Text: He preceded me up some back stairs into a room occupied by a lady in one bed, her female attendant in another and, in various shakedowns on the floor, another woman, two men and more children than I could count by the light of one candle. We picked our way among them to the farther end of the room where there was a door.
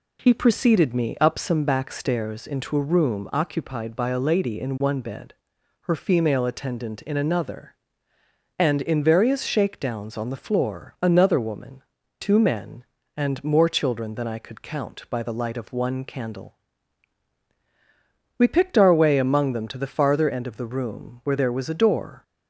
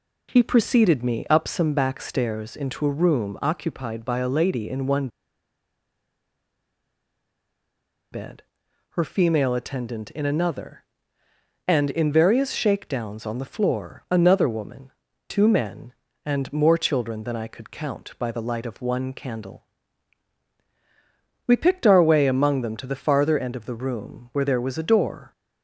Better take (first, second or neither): first